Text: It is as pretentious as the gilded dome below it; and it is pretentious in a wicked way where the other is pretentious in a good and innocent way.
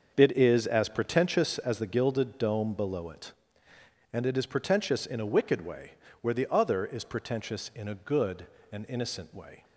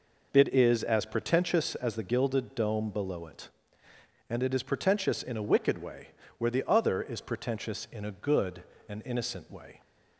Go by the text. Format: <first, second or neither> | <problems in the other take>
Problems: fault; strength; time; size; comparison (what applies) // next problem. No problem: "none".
second | gets quieter; strong; throughout; 11.5 dB // pauses between "way" and "where"; slight; at 5.9 s; 0.28 s long; slight in the second